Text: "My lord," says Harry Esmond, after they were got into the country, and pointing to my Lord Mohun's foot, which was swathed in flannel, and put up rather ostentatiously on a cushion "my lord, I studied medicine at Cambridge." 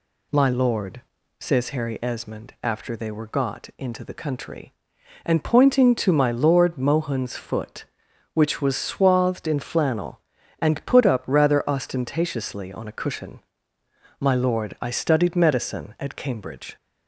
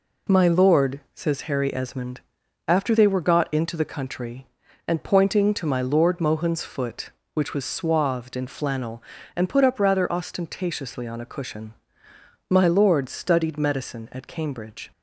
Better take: first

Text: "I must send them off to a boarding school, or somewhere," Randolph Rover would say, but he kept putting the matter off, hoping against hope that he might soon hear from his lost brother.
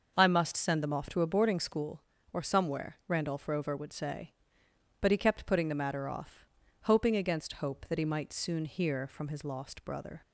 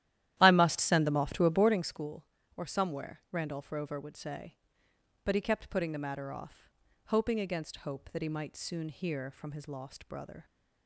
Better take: first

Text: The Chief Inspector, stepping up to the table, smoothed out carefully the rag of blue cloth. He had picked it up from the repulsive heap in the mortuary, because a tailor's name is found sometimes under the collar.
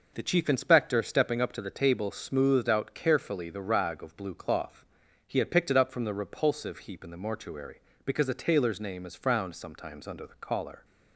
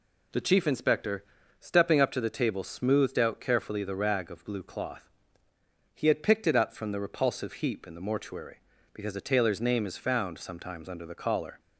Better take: second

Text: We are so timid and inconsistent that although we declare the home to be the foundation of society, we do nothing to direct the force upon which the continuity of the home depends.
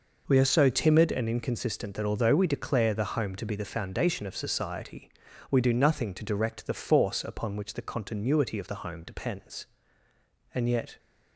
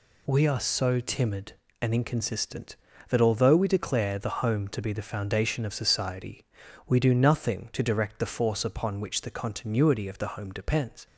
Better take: second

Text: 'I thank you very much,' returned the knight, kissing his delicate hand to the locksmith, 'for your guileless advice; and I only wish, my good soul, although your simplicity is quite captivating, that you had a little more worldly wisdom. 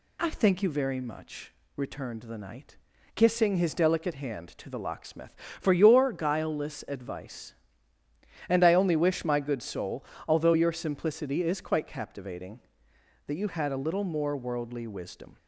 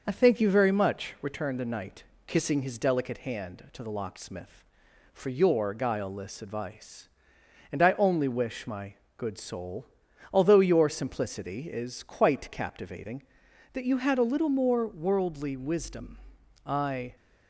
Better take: first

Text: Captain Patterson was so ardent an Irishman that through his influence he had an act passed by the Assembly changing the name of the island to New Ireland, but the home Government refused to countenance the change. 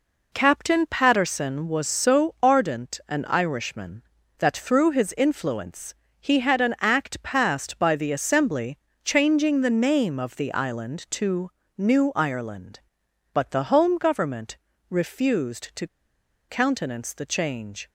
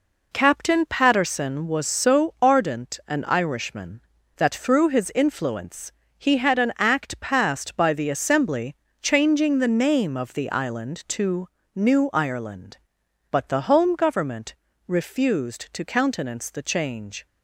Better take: second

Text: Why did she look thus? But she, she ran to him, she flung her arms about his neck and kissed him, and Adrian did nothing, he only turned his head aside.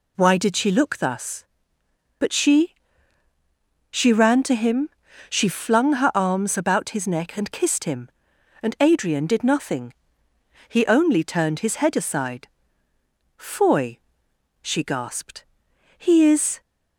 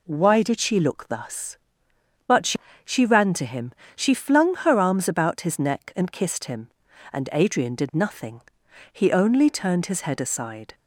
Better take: second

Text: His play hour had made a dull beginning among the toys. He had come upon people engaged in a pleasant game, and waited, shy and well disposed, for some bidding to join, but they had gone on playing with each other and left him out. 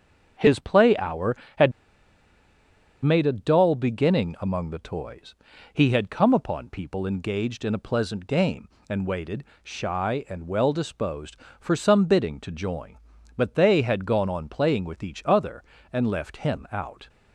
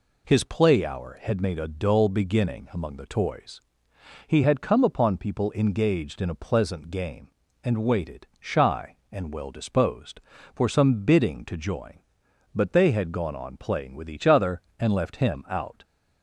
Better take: second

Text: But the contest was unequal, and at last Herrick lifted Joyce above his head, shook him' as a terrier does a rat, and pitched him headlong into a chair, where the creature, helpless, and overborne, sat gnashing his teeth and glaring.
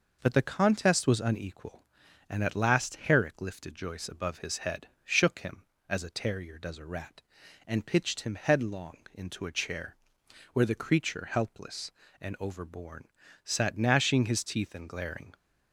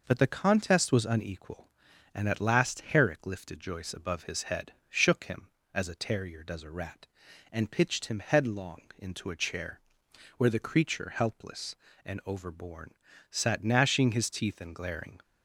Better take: neither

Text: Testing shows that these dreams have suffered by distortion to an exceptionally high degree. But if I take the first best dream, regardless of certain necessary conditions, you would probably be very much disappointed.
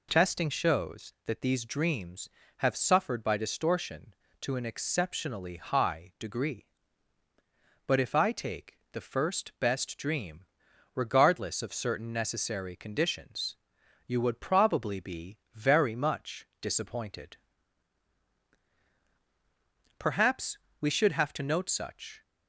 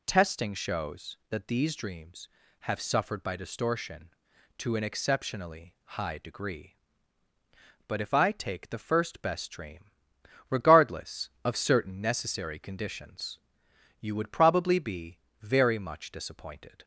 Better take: second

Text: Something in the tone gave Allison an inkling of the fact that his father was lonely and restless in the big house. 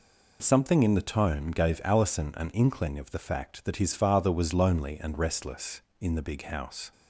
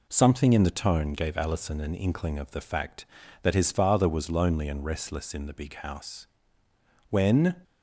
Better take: first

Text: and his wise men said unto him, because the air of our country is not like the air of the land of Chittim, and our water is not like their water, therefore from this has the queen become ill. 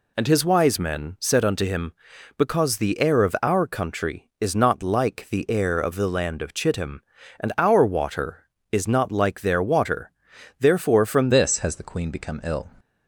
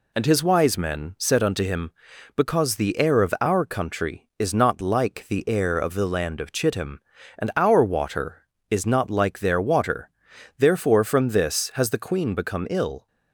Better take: second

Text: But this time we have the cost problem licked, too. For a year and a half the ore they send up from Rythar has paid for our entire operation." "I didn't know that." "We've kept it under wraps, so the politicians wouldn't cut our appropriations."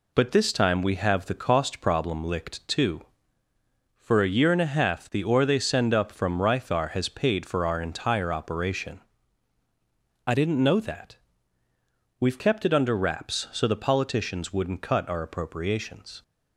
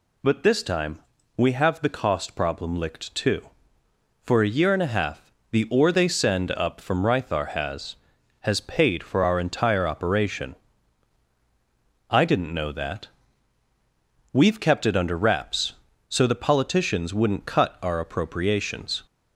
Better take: first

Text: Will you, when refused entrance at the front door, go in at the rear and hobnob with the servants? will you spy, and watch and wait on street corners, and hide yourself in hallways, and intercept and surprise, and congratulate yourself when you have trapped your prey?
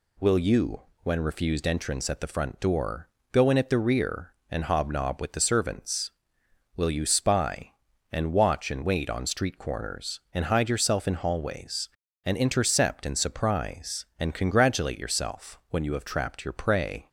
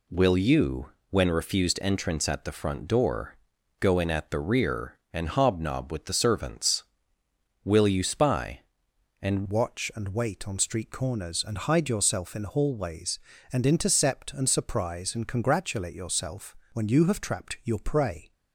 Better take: first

